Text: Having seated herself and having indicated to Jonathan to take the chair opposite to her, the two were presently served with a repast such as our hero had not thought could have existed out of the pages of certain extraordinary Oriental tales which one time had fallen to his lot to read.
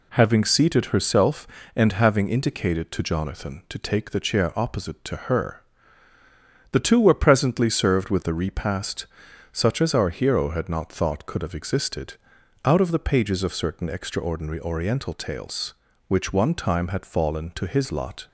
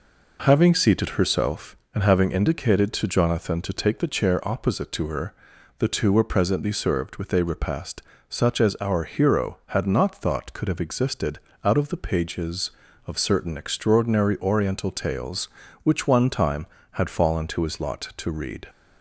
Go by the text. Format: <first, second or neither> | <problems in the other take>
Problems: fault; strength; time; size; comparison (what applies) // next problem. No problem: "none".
second | pauses between "repast" and "such"; noticeable; at 9.0 s; 0.48 s long; slight in the second // pauses between "existed" and "out"; noticeable; at 12.1 s; 0.50 s long; slight in the second // stops before "to read"; at 18.2 s